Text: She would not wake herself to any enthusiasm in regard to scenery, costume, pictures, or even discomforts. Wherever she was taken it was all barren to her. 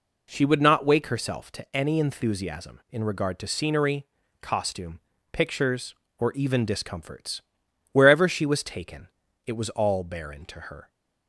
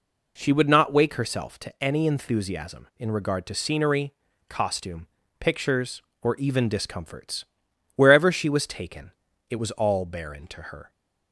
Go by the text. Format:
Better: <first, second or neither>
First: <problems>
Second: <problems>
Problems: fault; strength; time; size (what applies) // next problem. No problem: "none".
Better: neither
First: pauses between "taken" and "it"; slight; at 9.0 s; 0.36 s long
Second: pauses between "taken" and "it"; slight; at 9.1 s; 0.36 s long